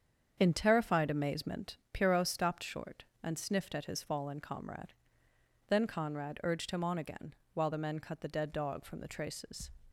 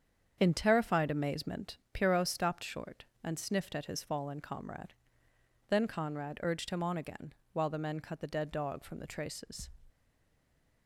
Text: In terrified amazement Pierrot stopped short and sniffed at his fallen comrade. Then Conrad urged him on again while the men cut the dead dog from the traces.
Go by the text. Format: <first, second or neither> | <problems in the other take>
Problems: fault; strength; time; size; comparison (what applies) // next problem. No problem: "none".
first | starts louder than the rest; strong; until 1.3 s; 7.5 dB; strong in the first // pauses between "again" and "while"; slight; at 7.3 s; 0.22 s long; slight in the first // stays silent after the last word; slight; from 9.9 s on; 0.9 s long